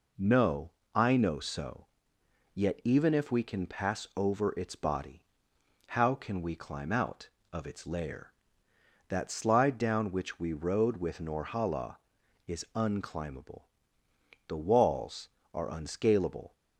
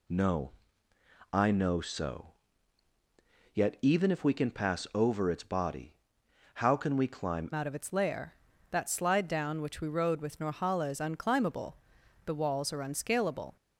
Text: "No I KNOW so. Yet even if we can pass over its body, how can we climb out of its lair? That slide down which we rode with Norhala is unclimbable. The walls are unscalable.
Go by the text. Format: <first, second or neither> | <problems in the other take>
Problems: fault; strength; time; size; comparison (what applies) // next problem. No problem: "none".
first | pauses between "No" and "I"; noticeable; at 0.5 s; 0.82 s long; slight in the first // changes voice at "out"; from 7.5 s on; 6.0 s long